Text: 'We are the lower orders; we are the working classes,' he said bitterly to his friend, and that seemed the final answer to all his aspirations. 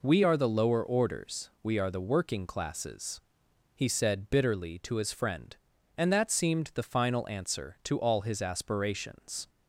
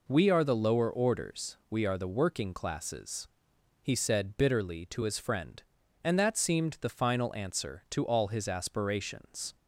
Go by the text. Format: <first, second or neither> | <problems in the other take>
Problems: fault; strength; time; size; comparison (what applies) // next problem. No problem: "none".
neither | none